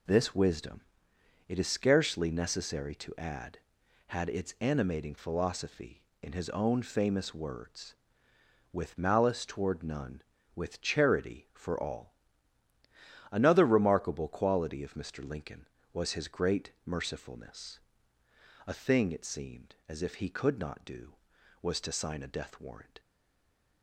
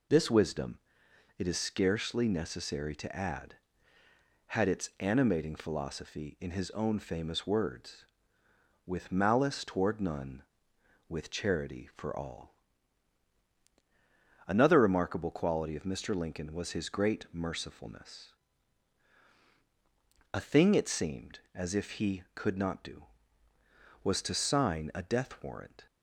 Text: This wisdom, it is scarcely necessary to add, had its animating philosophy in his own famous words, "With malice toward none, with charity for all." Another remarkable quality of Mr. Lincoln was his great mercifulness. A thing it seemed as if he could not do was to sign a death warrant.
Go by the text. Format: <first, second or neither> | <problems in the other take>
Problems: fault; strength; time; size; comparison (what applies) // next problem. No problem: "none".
second | stays silent after the last word; slight; from 22.9 s on; 0.9 s long